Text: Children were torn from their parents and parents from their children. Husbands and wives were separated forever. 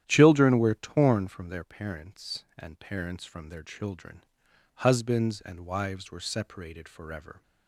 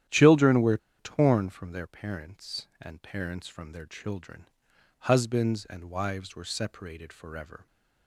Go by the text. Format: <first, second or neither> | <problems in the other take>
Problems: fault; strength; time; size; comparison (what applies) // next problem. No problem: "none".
first | starts louder than the rest; strong; until 1.3 s; 11 dB; strong in the first // pauses between "were" and "torn"; slight; at 0.7 s; 0.21 s long